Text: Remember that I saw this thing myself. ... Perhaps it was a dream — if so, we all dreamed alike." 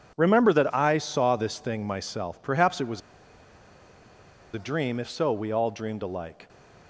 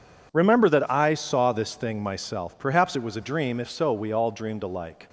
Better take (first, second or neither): second